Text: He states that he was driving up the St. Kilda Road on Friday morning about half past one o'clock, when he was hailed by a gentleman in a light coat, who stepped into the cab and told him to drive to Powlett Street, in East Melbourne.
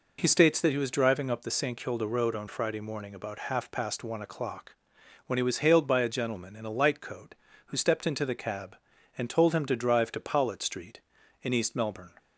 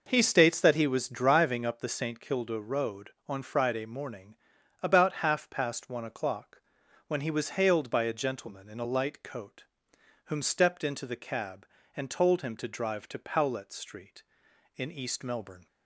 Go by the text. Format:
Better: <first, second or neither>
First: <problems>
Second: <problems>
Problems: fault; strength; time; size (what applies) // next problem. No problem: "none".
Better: first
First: none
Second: pauses between "morning" and "about"; at 4.3 s; 0.44 s long // says "whom" for "who"; at 10.2 s